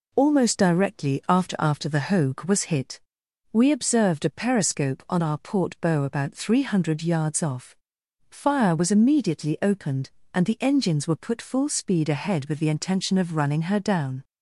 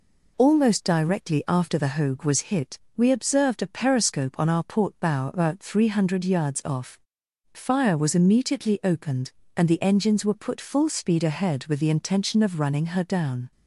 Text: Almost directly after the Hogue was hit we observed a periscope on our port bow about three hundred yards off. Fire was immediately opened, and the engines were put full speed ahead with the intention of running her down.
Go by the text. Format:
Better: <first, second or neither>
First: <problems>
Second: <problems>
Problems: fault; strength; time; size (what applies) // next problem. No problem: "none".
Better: second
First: says "after" twice; at 1.5 s // pauses between "hit" and "we"; noticeable; at 2.9 s; 0.54 s long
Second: pauses between "hit" and "we"; slight; at 2.7 s; 0.18 s long